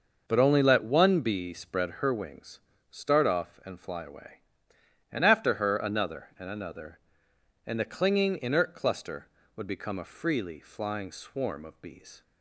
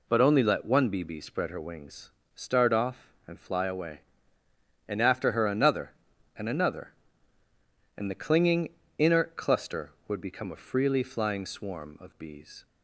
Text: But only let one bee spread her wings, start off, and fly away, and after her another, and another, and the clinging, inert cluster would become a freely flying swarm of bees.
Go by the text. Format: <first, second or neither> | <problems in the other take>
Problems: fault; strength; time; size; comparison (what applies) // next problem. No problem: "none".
first | says "bee" twice; at 1.0 s